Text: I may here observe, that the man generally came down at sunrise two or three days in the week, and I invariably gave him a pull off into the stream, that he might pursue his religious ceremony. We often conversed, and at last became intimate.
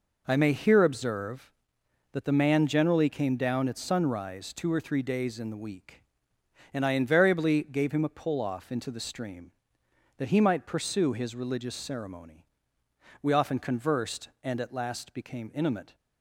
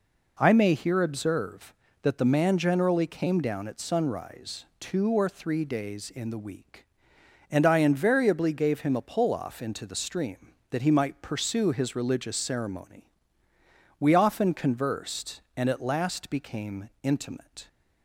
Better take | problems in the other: neither | none

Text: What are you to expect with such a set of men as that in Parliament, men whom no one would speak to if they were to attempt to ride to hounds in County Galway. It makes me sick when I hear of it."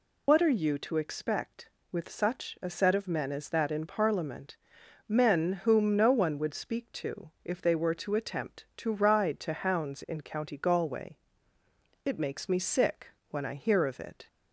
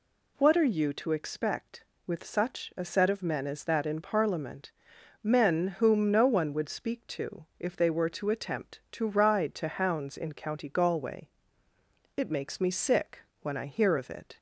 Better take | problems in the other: second | loses the start of "What"; at 0.2 s; 65 ms // pauses between "to" and "if"; slight; at 7.2 s; 0.16 s long; slight in the second // pauses between "sick" and "when"; slight; at 13.0 s; 0.22 s long; slight in the second

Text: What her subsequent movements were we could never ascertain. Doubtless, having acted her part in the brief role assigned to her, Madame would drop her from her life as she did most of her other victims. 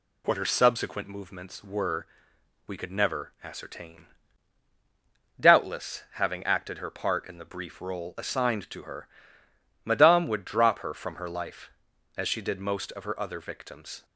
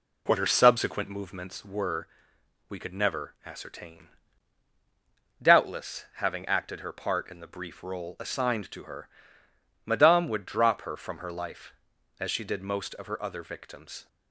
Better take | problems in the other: first | starts louder than the rest; slight; until 1.8 s; 2.5 dB // pauses between "were" and "we"; noticeable; at 2.0 s; 0.60 s long; noticeable in the first

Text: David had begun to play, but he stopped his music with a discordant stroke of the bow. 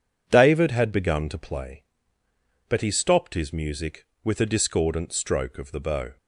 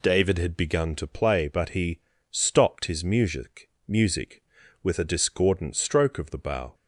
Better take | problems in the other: first | pauses between "he" and "stopped"; slight; at 2.0 s; 0.30 s long // says "music" twice; at 3.8 s

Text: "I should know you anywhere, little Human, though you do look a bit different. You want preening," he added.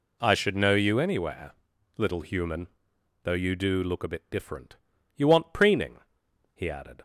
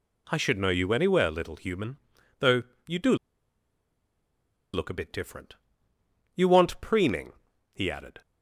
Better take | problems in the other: first | pauses between "though" and "you"; slight; at 2.6 s; 0.24 s long // pauses between "do" and "look"; strong; at 3.1 s; 1.5 s long

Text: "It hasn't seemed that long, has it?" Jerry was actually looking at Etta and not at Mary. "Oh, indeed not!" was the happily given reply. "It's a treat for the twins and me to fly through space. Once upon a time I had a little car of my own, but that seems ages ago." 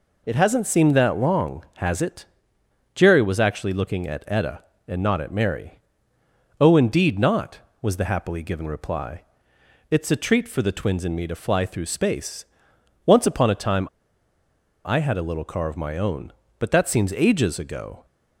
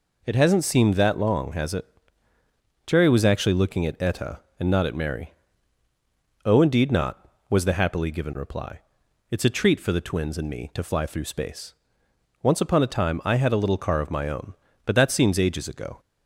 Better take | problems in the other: second | pauses between "time" and "I"; noticeable; at 13.8 s; 0.97 s long

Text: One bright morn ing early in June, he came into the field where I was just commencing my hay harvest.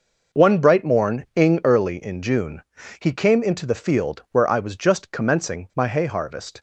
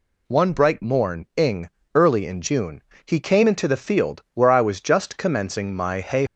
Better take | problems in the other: first | pauses between "ing" and "early"; slight; at 1.6 s; 0.24 s long // stops before "harvest"; at 6.2 s

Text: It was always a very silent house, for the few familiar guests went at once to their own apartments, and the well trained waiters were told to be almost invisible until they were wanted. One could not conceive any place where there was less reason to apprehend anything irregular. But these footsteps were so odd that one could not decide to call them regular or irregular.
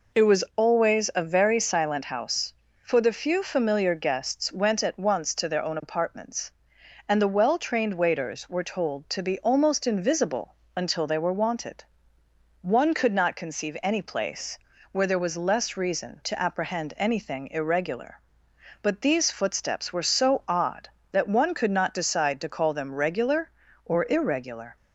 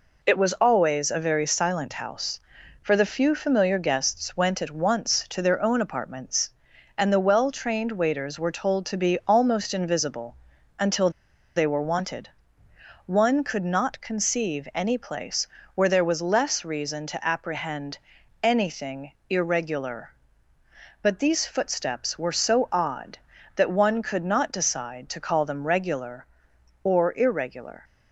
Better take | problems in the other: first | pauses between "invisible" and "until"; at 10.3 s; 0.42 s long; slight in the first // pauses between "until" and "they"; noticeable; at 11.0 s; 0.46 s long // pauses between "place" and "where"; slight; at 15.4 s; 0.30 s long; slight in the first // pauses between "apprehend" and "anything"; at 17.9 s; 0.42 s long // pauses between "anything" and "irregular"; slight; at 19.1 s; 0.18 s long

